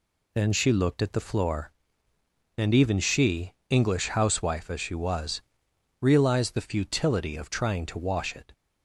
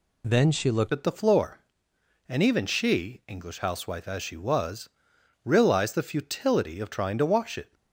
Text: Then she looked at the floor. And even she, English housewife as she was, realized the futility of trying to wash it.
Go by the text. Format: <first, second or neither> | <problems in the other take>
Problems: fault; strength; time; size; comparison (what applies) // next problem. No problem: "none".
first | changes voice at "at"; from 0.9 s on; 6.8 s long